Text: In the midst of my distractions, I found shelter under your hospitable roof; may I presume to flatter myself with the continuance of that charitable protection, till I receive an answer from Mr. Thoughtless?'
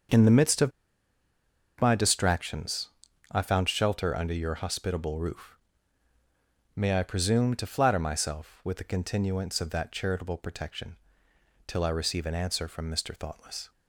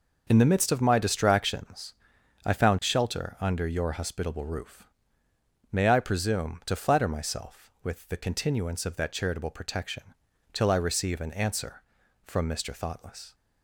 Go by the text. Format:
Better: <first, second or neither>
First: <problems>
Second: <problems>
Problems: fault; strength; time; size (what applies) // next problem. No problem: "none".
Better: second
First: starts louder than the rest; until 2.2 s; 6.5 dB // pauses between "of" and "my"; at 0.7 s; 1.0 s long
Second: none